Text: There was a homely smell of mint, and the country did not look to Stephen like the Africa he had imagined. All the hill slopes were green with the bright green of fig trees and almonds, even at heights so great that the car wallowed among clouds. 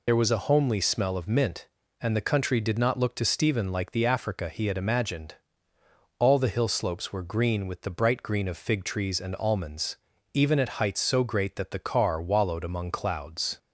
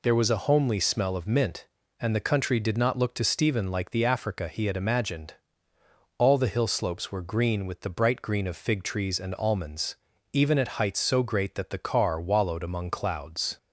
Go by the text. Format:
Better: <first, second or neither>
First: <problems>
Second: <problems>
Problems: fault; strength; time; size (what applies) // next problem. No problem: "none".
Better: second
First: loses the start of "There"; at 0.0 s; 40 ms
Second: none